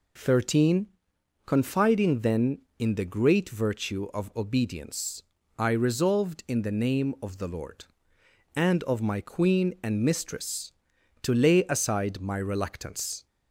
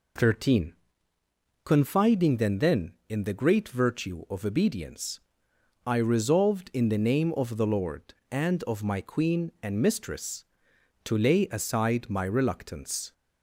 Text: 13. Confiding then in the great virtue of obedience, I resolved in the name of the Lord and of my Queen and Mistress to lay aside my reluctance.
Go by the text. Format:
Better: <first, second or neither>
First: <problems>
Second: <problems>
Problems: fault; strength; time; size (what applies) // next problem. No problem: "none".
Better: first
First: none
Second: says "then" twice; at 2.5 s